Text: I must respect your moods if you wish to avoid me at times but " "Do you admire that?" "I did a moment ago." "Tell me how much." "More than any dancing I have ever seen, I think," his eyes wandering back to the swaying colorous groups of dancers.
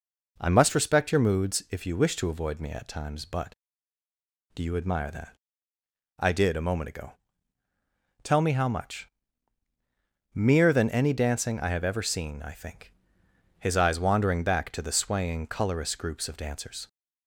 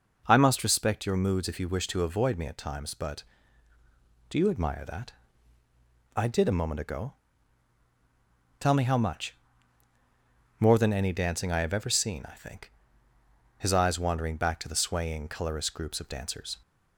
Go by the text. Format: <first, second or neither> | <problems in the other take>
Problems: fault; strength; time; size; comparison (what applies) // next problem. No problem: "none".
second | says "Mere" for "More"; at 10.3 s